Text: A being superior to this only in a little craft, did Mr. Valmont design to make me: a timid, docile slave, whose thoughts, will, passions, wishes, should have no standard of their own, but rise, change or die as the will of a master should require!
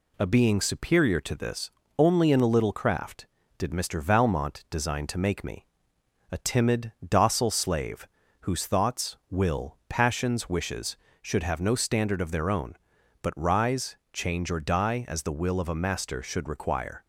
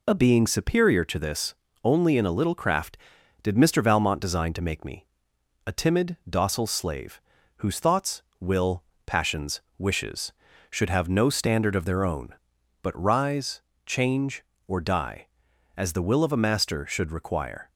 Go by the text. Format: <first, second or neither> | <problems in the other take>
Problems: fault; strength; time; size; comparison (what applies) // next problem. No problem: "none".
neither | pauses between "this" and "only"; slight; the same in both